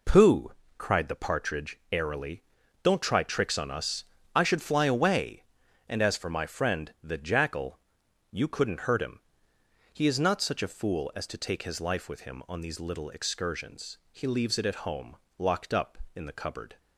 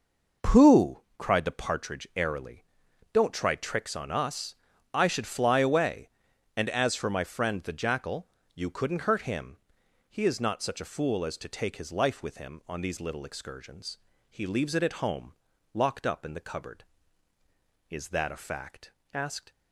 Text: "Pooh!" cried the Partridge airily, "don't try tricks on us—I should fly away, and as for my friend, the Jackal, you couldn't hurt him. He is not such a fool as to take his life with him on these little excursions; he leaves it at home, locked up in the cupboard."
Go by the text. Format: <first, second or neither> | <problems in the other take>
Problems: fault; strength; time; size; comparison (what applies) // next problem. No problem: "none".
first | goes on to say "Is that a fact asked"; from 17.8 s on; 1.6 s long